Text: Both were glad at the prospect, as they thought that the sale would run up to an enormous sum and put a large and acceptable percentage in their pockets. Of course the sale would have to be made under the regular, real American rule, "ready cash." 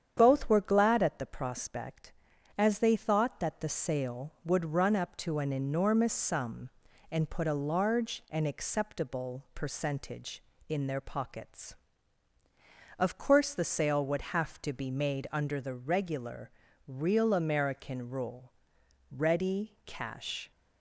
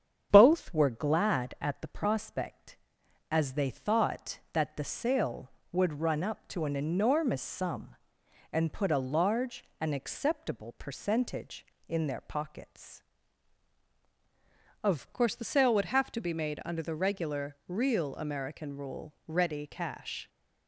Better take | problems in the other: first | starts louder than the rest; strong; until 1.3 s; 8 dB; strong in the first // changes voice at "course"; from 15.1 s on; 5.1 s long

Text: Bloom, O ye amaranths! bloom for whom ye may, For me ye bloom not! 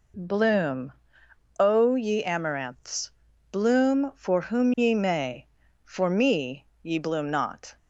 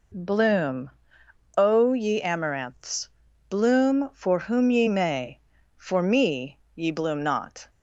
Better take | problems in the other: neither | pauses between "me" and "ye"; slight; the same in both

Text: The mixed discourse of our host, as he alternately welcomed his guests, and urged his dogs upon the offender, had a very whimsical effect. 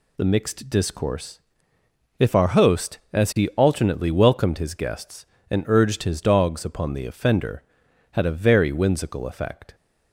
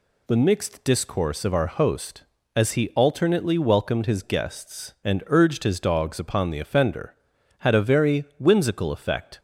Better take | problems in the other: second | says "if" for "of"; at 2.1 s

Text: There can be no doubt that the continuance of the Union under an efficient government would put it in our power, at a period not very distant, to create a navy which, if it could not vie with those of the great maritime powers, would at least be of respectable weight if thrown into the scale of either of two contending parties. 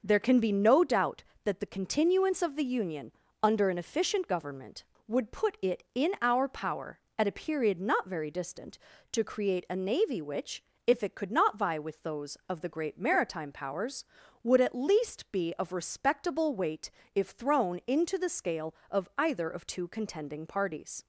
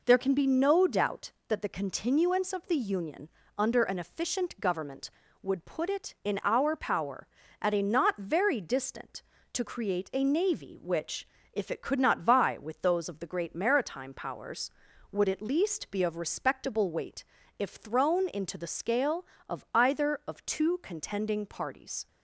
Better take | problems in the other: first | pauses between "Union" and "under"; slight; at 3.2 s; 0.28 s long; slight in the first // skips "period"; at 7.8 s // pauses between "weight" and "if"; slight; at 17.2 s; 0.36 s long; slight in the first

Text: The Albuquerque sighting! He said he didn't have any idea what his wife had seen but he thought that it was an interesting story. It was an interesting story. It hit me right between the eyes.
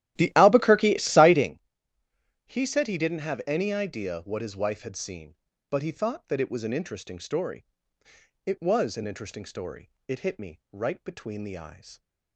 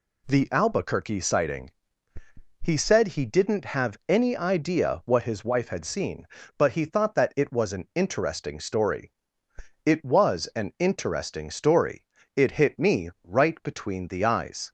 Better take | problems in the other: second | starts louder than the rest; strong; until 1.5 s; 13 dB

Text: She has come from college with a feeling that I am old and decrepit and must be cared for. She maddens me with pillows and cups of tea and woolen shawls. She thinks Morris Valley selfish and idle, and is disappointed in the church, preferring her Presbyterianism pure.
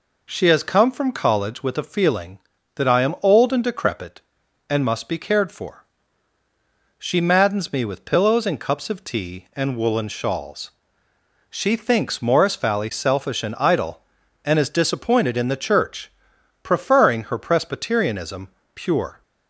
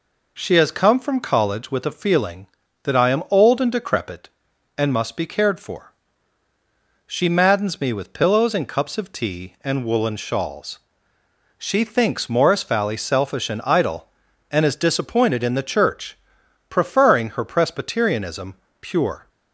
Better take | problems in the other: neither | pauses between "Presbyterianism" and "pure"; slight; the same in both

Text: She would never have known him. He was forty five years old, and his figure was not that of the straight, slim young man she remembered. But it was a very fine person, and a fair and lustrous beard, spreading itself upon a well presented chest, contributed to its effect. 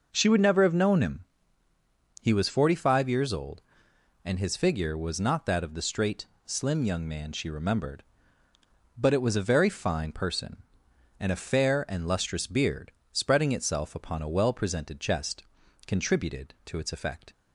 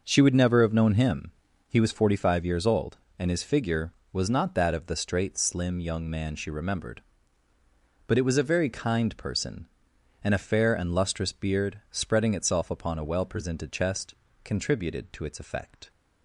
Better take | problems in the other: first | says "kind" for "fine"; at 8.6 s

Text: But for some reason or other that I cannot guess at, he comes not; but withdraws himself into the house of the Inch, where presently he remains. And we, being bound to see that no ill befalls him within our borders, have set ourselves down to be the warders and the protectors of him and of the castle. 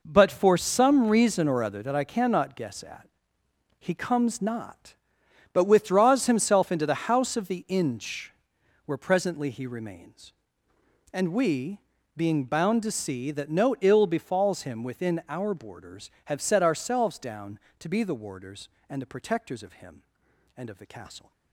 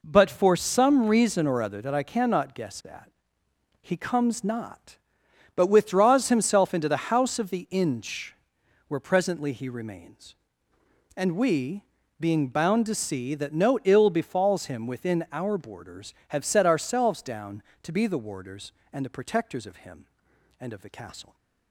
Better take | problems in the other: second | gets quieter; strong; throughout; 11 dB

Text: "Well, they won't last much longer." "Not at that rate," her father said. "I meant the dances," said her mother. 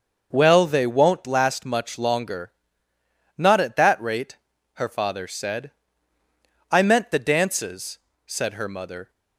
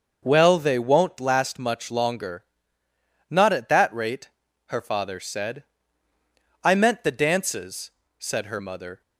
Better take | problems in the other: neither | starts louder than the rest; the same in both

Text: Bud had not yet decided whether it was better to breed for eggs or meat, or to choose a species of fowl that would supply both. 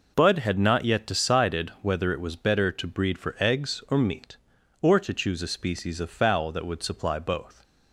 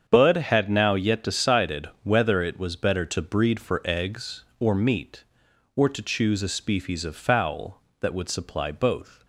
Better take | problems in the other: first | starts louder than the rest; strong; until 1.0 s; 7.5 dB // says "now" for "not"; at 0.6 s

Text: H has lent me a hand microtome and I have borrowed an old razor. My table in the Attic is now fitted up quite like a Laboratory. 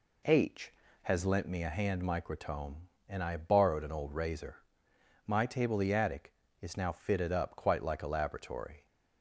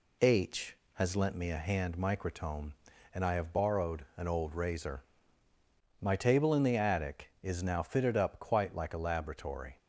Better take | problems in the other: second | skips "in"; at 5.7 s

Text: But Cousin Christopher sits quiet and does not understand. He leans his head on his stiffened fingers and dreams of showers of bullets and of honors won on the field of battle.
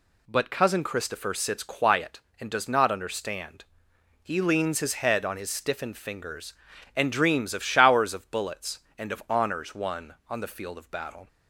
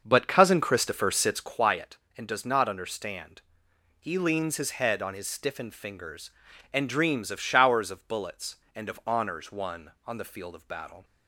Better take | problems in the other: first | starts louder than the rest; until 1.6 s; 6.5 dB

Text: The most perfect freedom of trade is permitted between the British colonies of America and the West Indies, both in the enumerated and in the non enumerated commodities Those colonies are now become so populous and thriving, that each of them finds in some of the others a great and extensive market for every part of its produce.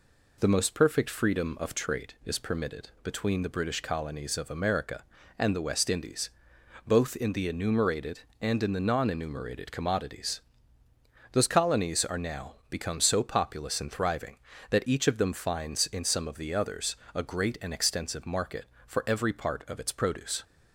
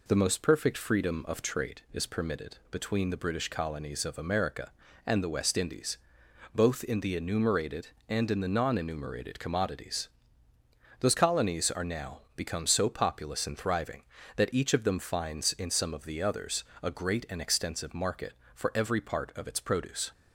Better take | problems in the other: neither | pauses between "commodities" and "Those"; noticeable; the same in both // pauses between "now" and "become"; slight; the same in both // pauses between "others" and "a"; slight; the same in both

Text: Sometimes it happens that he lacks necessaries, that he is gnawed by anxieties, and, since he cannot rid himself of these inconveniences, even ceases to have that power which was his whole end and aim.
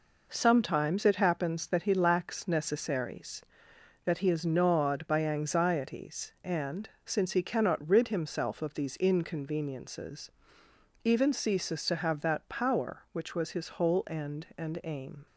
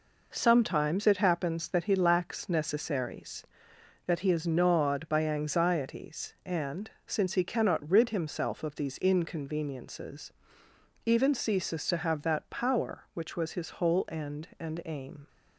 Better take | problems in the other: neither | none

